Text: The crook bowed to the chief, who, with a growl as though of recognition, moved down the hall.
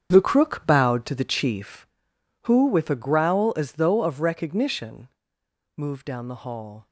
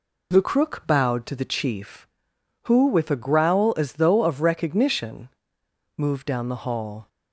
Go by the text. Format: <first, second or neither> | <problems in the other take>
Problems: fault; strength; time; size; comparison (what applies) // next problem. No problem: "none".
second | gets quieter; strong; throughout; 12.5 dB